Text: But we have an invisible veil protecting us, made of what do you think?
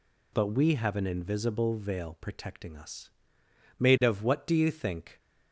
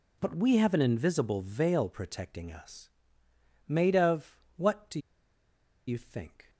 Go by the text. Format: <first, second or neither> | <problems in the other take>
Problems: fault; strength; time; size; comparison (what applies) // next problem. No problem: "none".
first | pauses between "of" and "what"; slight; at 4.3 s; 0.20 s long // pauses between "do" and "you"; noticeable; at 4.9 s; 0.88 s long